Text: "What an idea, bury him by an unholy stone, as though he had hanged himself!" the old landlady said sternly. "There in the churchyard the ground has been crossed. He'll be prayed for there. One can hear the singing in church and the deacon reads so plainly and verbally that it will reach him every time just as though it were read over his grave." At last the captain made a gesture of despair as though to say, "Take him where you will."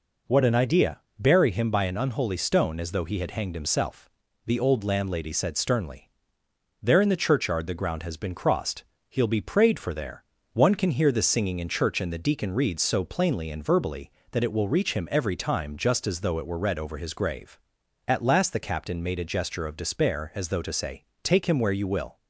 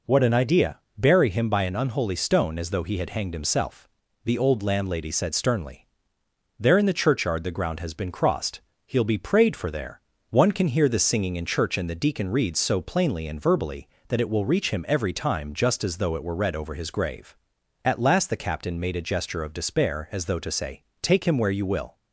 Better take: neither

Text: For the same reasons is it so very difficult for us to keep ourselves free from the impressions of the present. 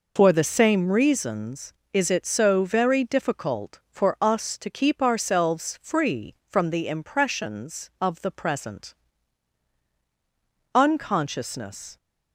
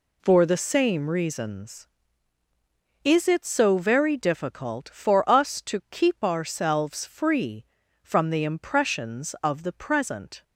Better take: second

